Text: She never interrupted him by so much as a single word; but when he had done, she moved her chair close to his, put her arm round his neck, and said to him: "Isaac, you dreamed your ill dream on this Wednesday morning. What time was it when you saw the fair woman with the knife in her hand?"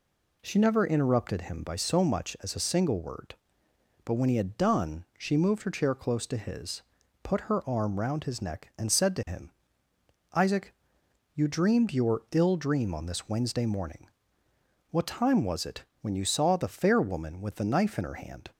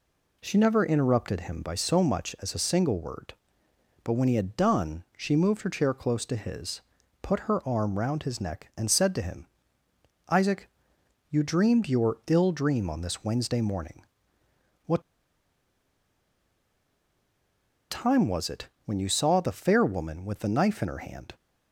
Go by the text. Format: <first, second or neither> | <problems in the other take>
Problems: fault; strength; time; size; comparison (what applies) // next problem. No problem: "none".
first | pauses between "What" and "time"; strong; at 15.0 s; 2.8 s long // pauses between "it" and "when"; slight; at 18.6 s; 0.16 s long; slight in the first